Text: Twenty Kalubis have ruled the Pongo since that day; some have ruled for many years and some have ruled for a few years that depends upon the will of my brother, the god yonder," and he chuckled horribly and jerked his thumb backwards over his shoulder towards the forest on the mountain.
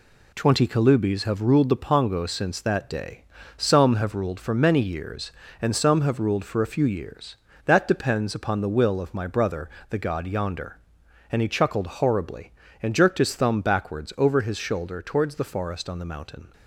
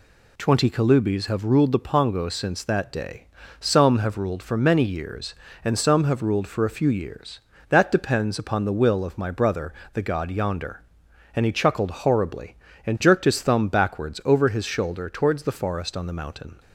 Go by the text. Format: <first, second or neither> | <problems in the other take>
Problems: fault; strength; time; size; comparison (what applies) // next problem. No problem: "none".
second | gets quieter; noticeable; throughout; 6 dB